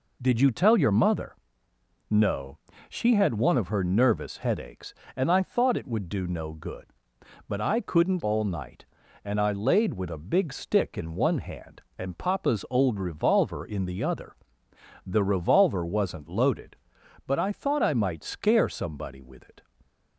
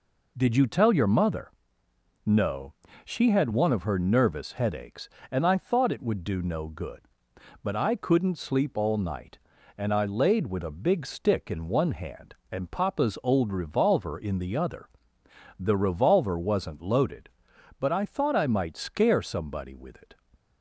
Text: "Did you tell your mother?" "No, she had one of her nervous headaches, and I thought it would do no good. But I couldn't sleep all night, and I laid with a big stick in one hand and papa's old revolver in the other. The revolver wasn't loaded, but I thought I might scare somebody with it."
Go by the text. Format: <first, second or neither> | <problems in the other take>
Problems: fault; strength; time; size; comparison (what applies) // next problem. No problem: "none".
second | skips "sleep"; at 8.2 s